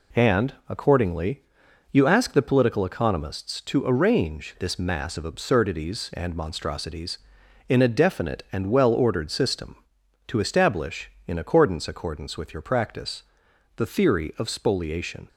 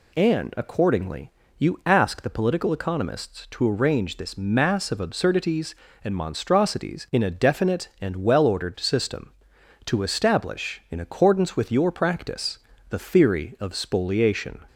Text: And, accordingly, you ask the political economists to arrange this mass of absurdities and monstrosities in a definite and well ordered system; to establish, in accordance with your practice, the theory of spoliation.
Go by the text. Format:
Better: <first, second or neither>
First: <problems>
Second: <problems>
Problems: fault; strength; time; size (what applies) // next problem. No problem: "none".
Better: second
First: says "accordance" twice; at 11.8 s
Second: none